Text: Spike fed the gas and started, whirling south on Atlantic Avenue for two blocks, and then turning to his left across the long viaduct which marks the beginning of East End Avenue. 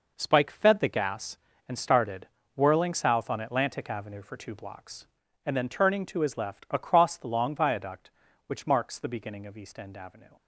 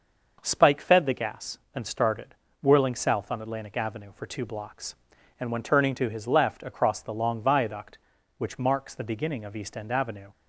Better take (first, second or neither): first